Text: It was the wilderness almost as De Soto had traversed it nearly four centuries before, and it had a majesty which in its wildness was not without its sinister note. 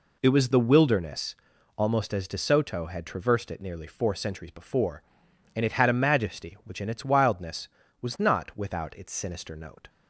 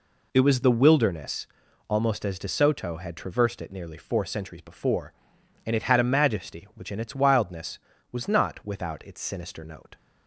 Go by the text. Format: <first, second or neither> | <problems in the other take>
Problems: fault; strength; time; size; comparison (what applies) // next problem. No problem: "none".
neither | pauses between "wilderness" and "almost"; the same in both